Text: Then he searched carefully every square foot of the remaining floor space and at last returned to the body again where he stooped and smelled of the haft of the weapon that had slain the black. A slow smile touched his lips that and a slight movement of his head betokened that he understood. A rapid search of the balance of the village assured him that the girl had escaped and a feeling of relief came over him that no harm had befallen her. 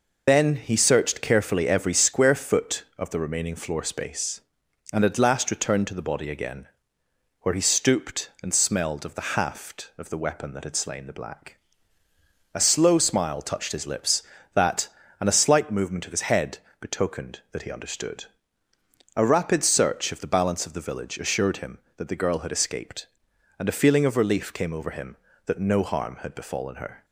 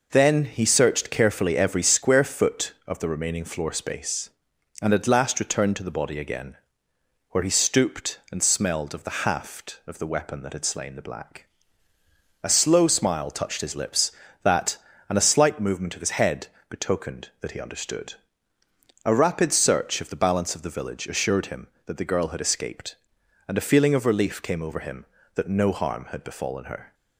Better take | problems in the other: second | loses the start of "Then"; at 0.2 s; 45 ms // pauses between "again" and "where"; noticeable; at 6.6 s; 0.74 s long; noticeable in the second // pauses between "head" and "betokened"; slight; at 16.5 s; 0.22 s long; slight in the second

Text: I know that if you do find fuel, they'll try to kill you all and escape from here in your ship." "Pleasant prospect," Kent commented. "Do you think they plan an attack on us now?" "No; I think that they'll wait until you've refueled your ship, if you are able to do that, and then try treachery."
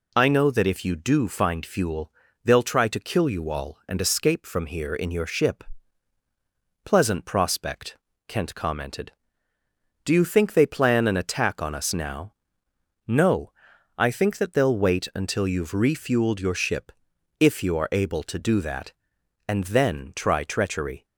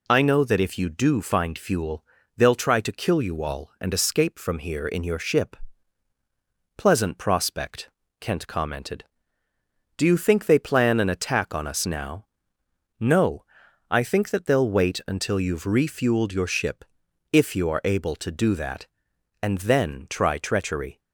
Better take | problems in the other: neither | none

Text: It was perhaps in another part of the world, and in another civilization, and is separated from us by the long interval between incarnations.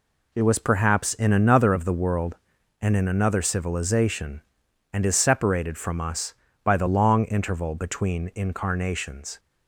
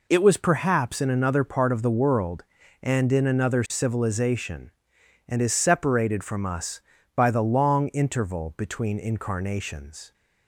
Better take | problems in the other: second | skips "part"; at 1.7 s

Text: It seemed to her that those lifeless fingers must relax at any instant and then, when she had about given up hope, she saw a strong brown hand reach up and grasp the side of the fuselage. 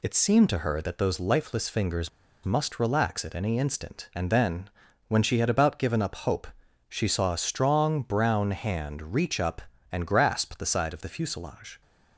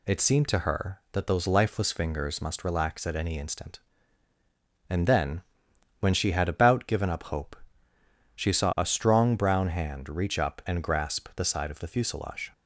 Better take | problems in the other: second | pauses between "fingers" and "must"; slight; at 2.0 s; 0.35 s long

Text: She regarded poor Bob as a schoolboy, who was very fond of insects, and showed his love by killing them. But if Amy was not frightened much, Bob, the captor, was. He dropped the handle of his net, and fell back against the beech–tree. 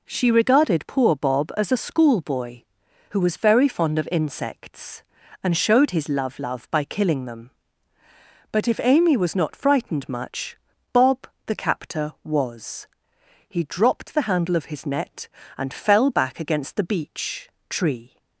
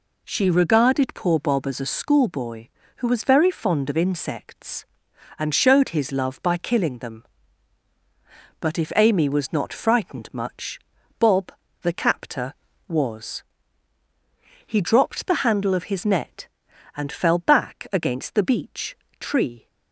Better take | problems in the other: second | says "love" twice; at 6.3 s

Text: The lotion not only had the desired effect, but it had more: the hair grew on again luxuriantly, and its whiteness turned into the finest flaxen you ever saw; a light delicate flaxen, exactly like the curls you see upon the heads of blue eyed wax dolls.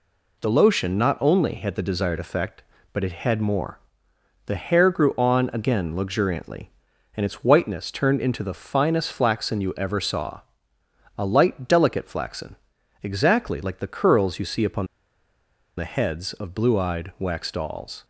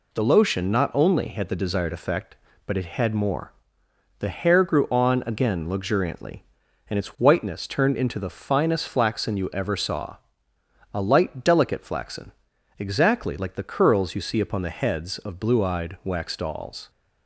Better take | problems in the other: second | pauses between "upon" and "the"; noticeable; at 14.8 s; 0.91 s long

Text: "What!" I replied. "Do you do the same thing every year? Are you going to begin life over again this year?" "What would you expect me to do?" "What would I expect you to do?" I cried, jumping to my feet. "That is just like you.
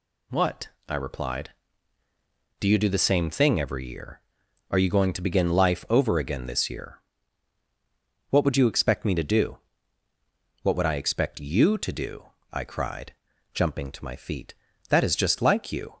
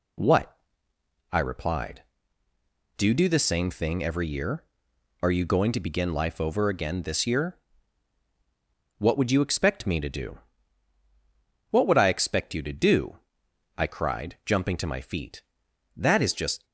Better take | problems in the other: first | stops before "like you"; at 16.6 s

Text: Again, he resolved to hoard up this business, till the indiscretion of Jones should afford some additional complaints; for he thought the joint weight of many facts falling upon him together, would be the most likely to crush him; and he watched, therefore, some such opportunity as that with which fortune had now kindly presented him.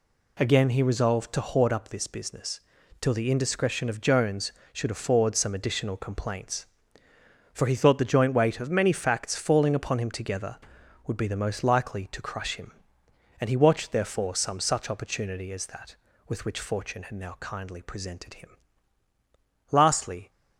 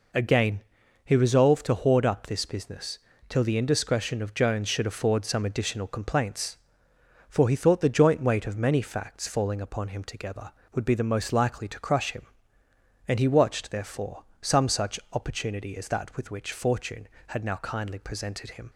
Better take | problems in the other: second | goes on to say "Lastly"; from 19.7 s on; 0.58 s long

